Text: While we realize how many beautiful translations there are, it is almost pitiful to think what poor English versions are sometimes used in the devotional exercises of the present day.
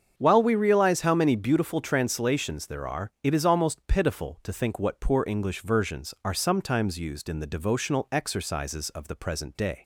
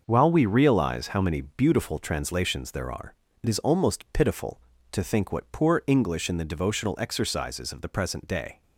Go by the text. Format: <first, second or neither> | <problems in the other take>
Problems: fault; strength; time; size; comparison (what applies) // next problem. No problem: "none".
first | starts louder than the rest; until 1.0 s; 6.5 dB; strong in the first // skips "versions are sometimes used"; at 6.2 s